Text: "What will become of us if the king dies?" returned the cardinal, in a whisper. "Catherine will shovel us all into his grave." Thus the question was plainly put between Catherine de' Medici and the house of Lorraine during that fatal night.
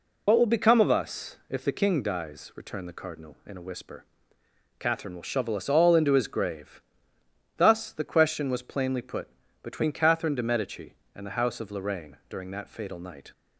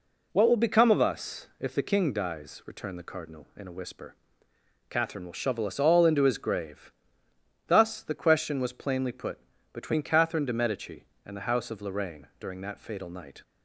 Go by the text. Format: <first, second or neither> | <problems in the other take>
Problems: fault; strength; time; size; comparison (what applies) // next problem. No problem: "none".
second | loses the start of "What"; at 0.2 s; 60 ms // pauses between "put" and "between"; slight; at 9.2 s; 0.32 s long; slight in the second